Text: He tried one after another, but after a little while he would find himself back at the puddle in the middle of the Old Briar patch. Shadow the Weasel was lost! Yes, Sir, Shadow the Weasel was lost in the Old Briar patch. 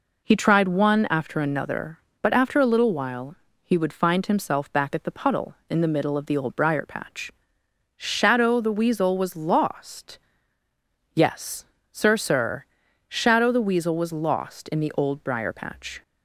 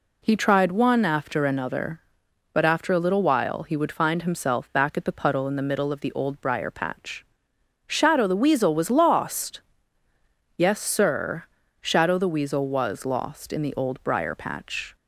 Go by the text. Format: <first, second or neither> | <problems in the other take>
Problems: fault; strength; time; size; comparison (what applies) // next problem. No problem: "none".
second | pauses between "while" and "he"; slight; at 3.3 s; 0.26 s long // says "Sir" twice; at 12.1 s